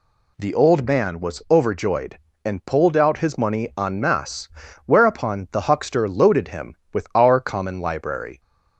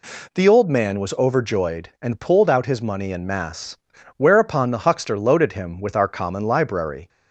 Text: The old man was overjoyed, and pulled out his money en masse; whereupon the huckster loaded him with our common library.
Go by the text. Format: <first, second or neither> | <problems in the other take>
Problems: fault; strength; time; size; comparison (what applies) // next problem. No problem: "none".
neither | none